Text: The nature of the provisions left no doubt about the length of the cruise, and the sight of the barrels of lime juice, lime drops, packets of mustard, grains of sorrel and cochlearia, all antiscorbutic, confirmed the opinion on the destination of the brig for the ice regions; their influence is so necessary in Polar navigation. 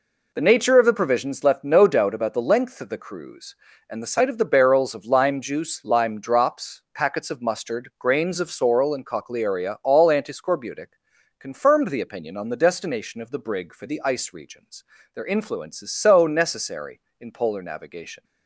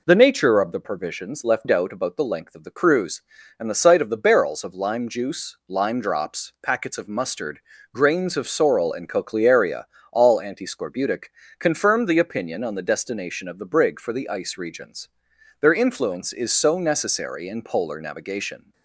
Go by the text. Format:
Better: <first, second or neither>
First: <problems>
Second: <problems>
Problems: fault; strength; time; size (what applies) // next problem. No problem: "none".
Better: first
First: none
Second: skips "no"; at 1.6 s